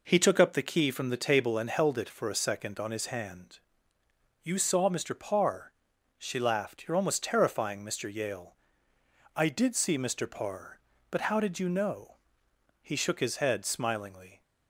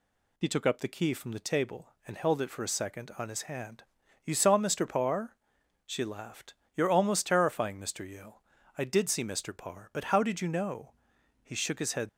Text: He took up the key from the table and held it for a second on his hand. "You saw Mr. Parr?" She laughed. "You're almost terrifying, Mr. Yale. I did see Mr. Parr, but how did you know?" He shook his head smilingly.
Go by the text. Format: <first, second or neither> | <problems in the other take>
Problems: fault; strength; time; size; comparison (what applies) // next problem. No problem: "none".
first | stops before "smilingly"; at 12.0 s